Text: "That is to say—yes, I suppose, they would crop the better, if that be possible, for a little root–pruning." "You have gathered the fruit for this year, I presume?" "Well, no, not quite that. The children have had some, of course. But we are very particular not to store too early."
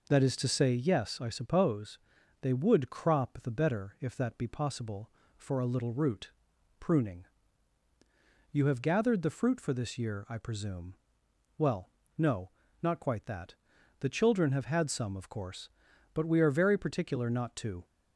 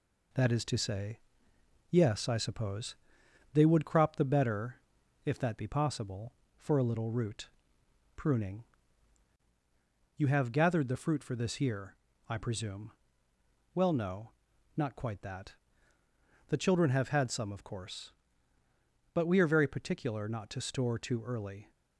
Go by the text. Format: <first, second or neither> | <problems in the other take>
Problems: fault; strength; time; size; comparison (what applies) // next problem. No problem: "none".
second | stops before "store too early"; at 17.8 s